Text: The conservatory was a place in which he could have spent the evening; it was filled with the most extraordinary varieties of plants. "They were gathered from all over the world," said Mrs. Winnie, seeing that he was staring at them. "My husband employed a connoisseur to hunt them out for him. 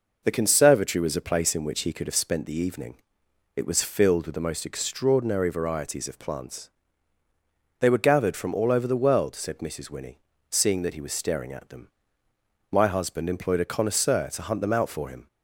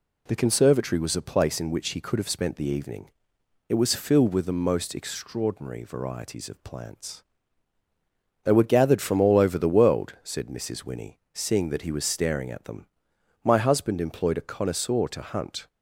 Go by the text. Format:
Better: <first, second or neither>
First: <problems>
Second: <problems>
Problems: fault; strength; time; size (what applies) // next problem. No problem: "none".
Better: first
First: none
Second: stops before "them out for him"; at 15.6 s